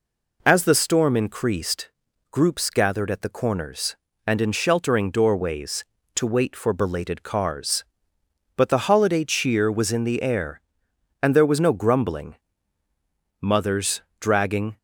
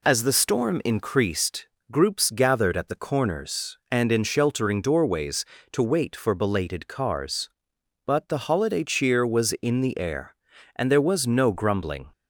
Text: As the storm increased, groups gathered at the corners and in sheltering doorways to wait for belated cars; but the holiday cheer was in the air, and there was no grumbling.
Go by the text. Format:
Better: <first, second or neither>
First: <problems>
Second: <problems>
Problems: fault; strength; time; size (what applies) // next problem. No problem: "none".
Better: second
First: goes on to say "Mothers dragging"; from 13.3 s on; 1.3 s long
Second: none